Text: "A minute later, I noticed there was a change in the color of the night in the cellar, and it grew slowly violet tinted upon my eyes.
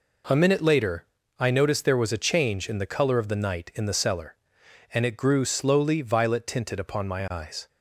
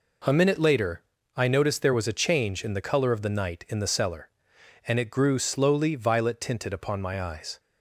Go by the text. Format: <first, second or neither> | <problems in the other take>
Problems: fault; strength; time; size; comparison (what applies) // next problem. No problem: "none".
neither | none